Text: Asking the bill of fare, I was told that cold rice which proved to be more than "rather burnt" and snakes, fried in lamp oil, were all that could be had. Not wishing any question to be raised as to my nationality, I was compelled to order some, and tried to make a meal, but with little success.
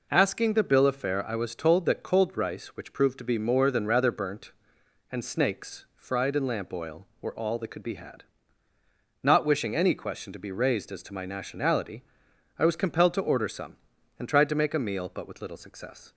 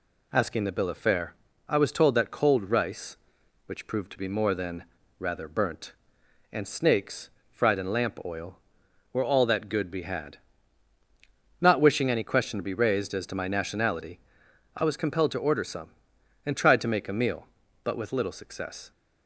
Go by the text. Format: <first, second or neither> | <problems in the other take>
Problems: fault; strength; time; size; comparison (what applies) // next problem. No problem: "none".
first | pauses between "than" and "rather"; slight; at 4.8 s; 0.36 s long // says "good" for "could"; at 9.6 s